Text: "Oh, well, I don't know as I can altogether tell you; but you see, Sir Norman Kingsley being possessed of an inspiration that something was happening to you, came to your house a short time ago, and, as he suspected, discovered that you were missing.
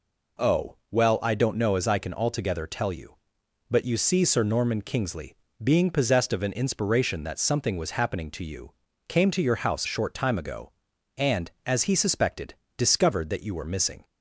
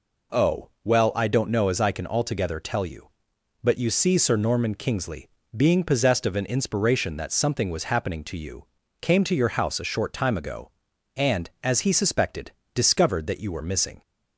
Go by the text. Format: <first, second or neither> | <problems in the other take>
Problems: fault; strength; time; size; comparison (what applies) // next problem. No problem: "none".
second | pauses between "Kingsley" and "being"; slight; at 5.3 s; 0.26 s long; slight in the second // skips "a"; at 9.8 s